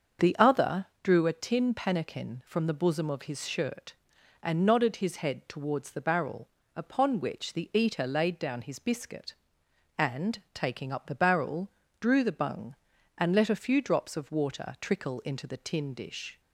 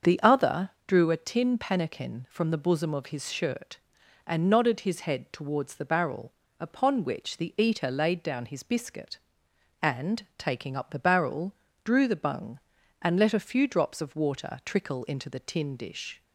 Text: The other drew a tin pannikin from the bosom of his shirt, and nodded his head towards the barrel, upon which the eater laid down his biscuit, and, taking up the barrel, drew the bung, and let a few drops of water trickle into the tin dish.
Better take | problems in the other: neither | starts louder than the rest; the same in both // pauses between "other" and "drew"; slight; the same in both

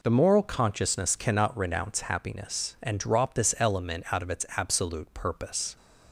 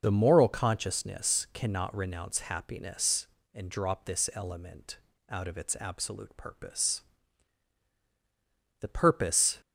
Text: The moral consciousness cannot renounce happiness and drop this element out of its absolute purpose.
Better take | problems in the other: first | pauses between "element" and "out"; slight; at 4.9 s; 0.32 s long // goes on to say "The purpose"; noticeable; from 8.8 s on; 0.80 s long

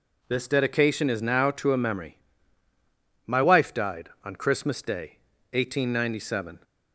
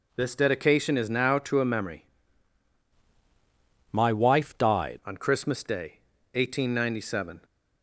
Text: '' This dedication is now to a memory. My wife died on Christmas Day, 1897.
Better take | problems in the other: first | changes voice from "My" to "died"; from 3.9 to 4.9 s; 1.0 s long

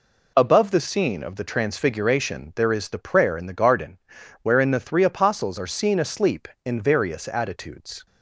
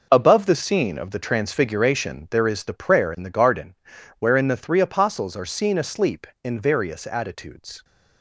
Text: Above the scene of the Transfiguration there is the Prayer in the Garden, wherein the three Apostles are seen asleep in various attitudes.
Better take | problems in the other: first | gets quieter; strong; throughout; 10.5 dB

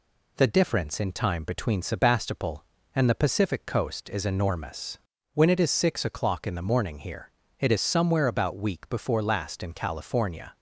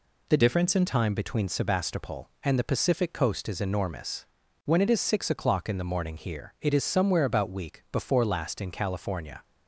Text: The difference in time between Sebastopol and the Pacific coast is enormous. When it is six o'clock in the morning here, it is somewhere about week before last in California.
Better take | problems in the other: first | changes voice from "difference" to "in"; from 0.3 to 0.8 s; 0.5 s long

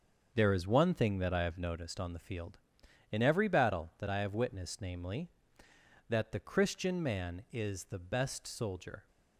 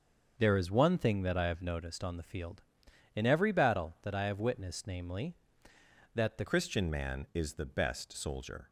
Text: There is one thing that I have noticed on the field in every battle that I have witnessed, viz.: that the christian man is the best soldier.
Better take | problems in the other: first | starts louder than the rest; until 1.3 s; 6.5 dB; also in the first // changes voice at "christian"; from 6.4 s on; 2.2 s long

